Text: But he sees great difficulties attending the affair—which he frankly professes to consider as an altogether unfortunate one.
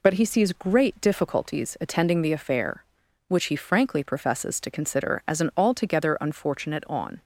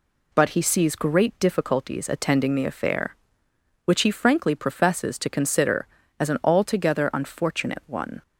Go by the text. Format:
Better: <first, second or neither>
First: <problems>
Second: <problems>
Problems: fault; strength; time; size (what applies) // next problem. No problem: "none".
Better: second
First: says "on" for "one"; at 6.8 s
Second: none